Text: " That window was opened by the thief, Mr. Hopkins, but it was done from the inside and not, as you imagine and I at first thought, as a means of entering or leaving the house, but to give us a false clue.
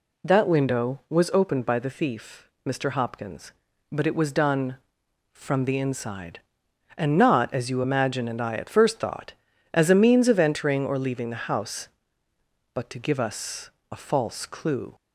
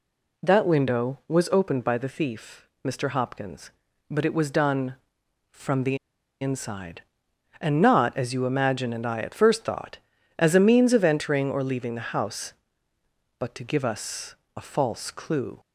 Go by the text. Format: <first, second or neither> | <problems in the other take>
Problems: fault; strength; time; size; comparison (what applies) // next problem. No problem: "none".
first | pauses between "the" and "inside"; at 5.9 s; 0.44 s long // pauses between "us" and "a"; slight; at 14.3 s; 0.20 s long; slight in the first